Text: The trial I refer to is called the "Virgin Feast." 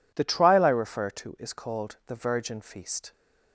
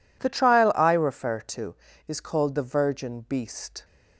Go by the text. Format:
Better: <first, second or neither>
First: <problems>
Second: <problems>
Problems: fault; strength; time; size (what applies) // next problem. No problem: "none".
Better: first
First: none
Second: says "Beast" for "Feast"; at 3.2 s